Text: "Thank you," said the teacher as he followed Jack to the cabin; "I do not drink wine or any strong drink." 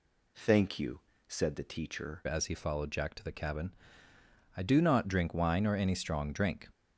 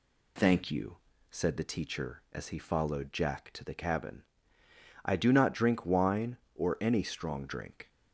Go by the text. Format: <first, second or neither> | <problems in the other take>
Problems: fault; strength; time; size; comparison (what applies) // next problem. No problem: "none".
second | changes voice at "as"; from 2.2 s on; 4.4 s long